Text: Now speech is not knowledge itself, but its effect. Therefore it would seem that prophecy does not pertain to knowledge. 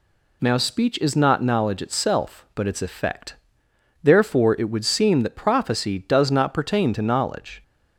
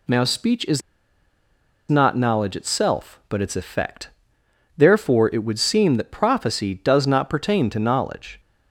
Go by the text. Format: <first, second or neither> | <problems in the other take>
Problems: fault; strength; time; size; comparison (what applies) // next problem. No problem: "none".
first | pauses between "is" and "not"; at 0.8 s; 1.0 s long